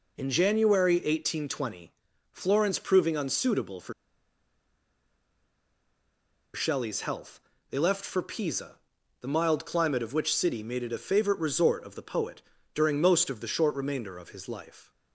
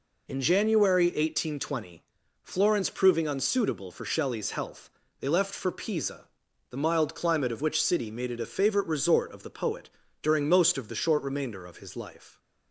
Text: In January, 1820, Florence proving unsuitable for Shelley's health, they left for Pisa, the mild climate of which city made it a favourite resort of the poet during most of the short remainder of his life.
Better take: second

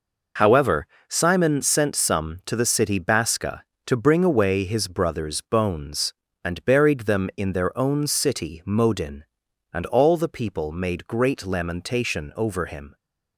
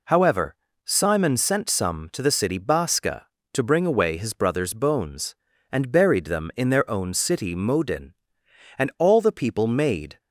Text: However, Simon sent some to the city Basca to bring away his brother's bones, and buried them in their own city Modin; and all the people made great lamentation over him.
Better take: first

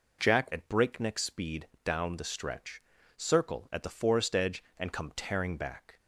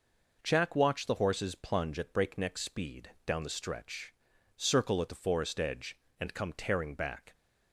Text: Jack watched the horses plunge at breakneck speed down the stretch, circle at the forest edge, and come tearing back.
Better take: second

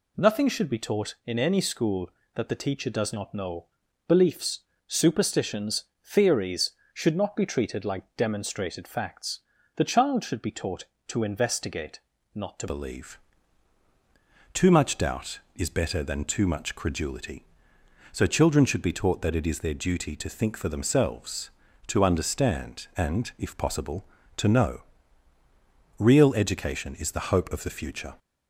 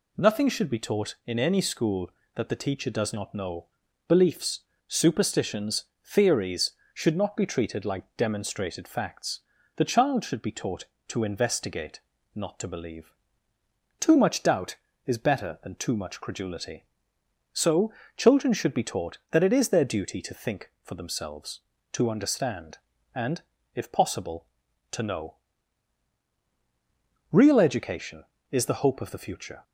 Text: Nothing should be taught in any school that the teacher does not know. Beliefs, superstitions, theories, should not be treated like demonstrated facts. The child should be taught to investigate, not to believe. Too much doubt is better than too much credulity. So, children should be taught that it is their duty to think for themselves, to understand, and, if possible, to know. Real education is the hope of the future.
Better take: second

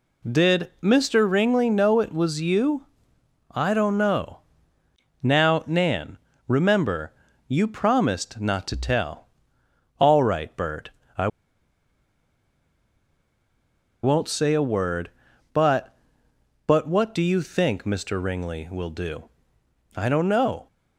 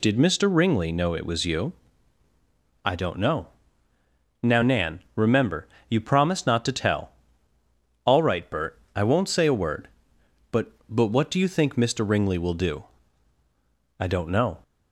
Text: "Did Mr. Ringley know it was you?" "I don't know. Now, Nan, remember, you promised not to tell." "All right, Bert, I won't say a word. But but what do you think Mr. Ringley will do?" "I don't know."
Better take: second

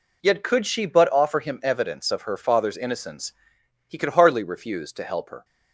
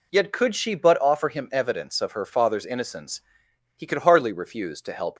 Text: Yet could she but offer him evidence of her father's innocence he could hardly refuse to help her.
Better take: first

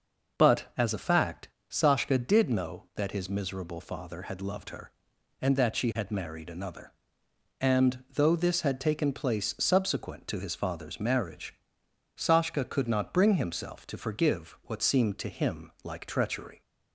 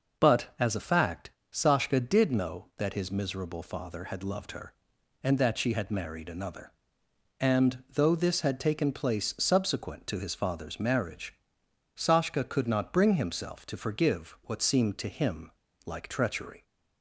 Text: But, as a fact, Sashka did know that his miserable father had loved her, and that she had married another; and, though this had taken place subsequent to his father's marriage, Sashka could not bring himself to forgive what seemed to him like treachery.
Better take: first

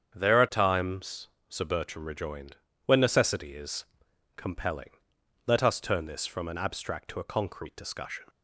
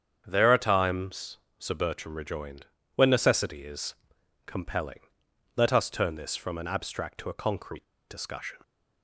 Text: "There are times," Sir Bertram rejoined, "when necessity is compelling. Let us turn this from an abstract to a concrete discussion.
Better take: first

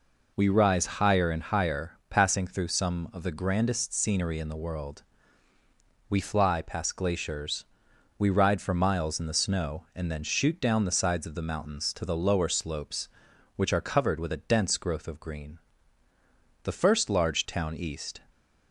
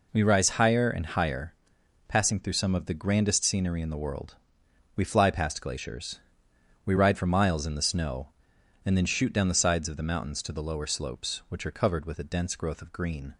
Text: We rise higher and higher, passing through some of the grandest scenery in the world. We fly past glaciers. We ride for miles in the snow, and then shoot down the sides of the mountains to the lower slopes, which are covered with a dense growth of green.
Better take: second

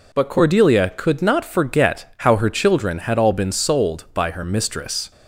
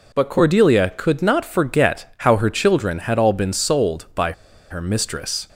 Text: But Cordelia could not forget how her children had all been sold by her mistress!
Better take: first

